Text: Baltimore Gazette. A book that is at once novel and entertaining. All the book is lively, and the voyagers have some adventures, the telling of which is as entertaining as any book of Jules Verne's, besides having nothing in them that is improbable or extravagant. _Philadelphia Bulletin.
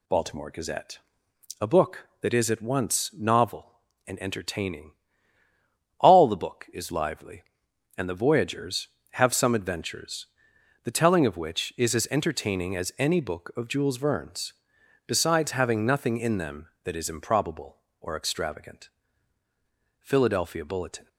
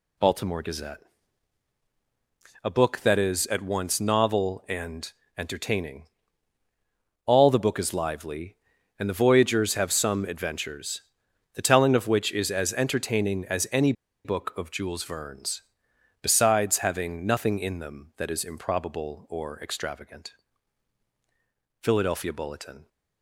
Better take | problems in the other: first | pauses between "and" and "entertaining"; slight; at 5.1 s; 0.24 s long // pauses between "any" and "book"; slight; at 13.9 s; 0.32 s long

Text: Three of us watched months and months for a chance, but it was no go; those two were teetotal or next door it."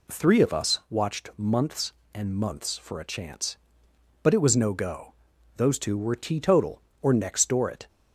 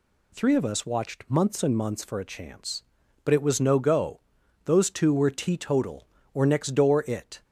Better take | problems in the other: neither | none

